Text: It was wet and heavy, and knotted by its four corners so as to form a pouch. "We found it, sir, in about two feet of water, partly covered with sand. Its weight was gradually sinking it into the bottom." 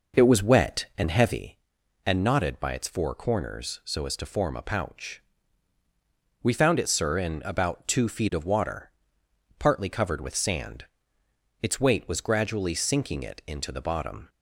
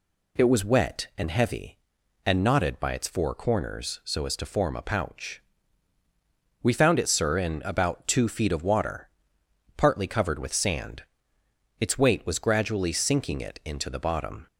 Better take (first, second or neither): second